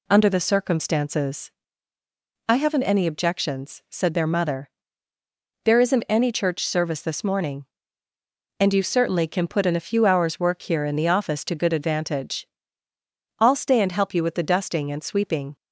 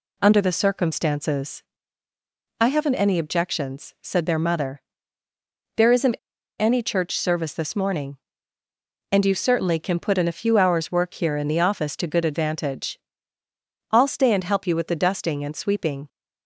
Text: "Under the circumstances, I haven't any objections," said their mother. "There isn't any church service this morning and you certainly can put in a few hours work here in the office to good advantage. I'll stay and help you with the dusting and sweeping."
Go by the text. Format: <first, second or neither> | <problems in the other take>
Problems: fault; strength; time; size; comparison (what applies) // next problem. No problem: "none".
first | pauses between "isn't" and "any"; at 6.1 s; 0.42 s long